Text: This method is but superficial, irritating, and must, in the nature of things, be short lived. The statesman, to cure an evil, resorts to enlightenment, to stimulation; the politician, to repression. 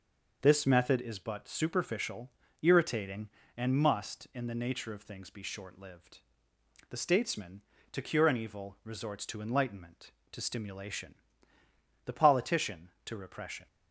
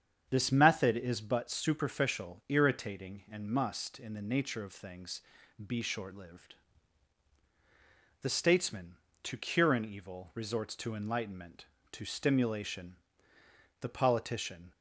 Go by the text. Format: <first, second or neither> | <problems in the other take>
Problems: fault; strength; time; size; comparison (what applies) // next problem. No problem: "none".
first | starts louder than the rest; strong; until 1.3 s; 7.5 dB // stops before "to repression"; at 14.7 s